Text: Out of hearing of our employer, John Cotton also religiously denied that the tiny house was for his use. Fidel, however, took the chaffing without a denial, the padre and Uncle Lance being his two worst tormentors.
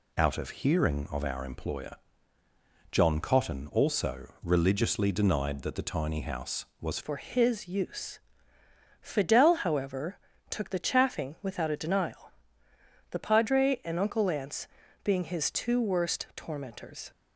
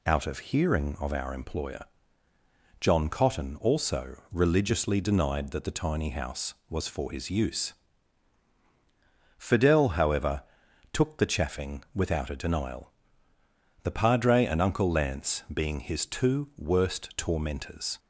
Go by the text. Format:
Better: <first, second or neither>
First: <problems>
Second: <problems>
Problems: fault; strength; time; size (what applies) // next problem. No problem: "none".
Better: second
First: pauses between "also" and "religiously"; slight; at 4.2 s; 0.16 s long // changes voice at "for"; from 7.0 s on; 10.1 s long // pauses between "Lance" and "being"; at 14.6 s; 0.38 s long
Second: pauses between "also" and "religiously"; slight; at 4.1 s; 0.16 s long